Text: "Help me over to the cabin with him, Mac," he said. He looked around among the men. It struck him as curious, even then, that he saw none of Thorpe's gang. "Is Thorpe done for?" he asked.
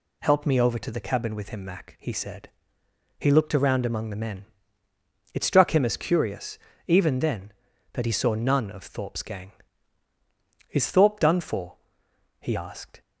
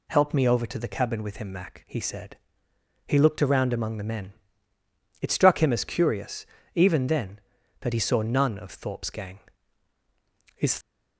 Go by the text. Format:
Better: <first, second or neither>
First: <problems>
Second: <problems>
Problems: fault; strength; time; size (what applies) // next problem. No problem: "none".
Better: first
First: none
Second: stops before "Thorpe done for he asked"; at 10.8 s